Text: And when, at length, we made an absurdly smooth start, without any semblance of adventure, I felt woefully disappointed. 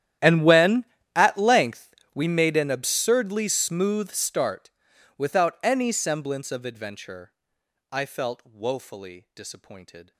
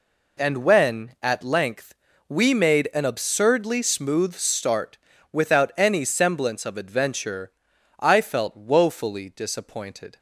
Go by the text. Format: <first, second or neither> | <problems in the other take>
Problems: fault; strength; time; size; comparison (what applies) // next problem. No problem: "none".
second | gets quieter; strong; throughout; 25 dB